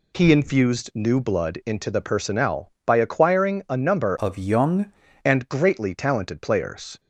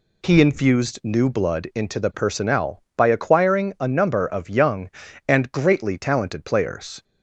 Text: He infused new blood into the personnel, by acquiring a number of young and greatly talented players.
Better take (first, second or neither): second